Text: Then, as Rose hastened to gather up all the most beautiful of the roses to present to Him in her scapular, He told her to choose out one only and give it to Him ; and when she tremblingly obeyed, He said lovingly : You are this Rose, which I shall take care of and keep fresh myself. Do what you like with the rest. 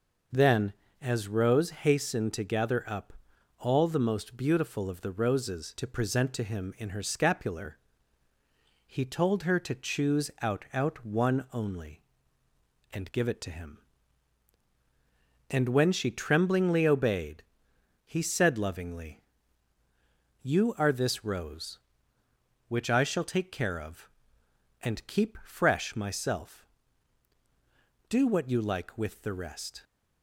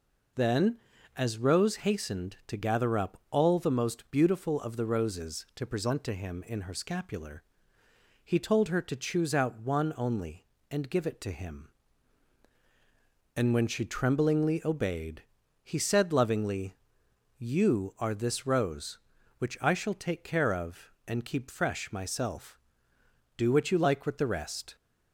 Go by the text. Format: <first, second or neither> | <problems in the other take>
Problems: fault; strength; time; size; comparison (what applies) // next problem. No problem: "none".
second | pauses between "up" and "all"; noticeable; at 3.1 s; 0.46 s long // says "out" twice; at 10.7 s